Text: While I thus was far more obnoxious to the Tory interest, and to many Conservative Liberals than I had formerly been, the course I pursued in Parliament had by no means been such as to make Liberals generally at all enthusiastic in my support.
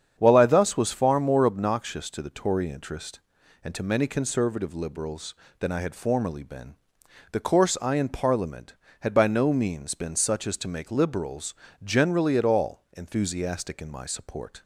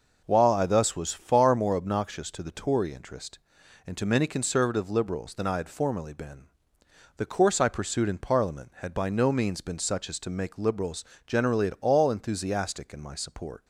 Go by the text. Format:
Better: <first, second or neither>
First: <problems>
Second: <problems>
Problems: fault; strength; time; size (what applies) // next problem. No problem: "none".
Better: second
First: starts louder than the rest; strong; until 1.1 s; 8 dB // skips "pursued"; at 7.9 s // pauses between "Liberals" and "generally"; slight; at 11.5 s; 0.30 s long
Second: pauses between "Liberals" and "generally"; slight; at 11.0 s; 0.24 s long